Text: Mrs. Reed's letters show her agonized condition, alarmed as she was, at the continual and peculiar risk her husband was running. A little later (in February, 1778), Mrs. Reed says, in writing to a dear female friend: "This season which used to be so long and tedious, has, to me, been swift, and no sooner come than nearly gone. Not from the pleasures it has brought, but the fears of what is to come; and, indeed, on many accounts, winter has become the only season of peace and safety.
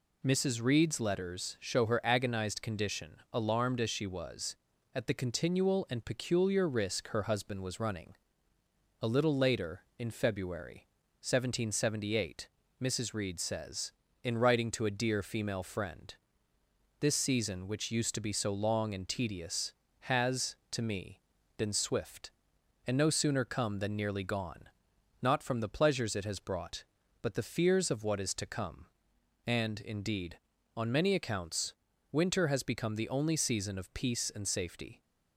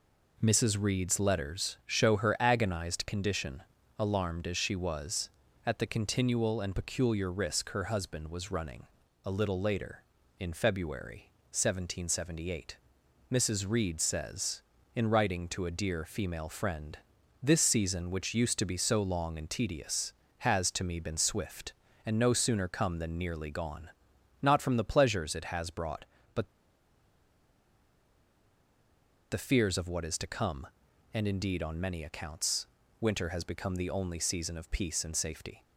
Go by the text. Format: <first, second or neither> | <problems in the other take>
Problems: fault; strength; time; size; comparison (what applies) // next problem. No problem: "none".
first | pauses between "but" and "the"; strong; at 26.4 s; 2.8 s long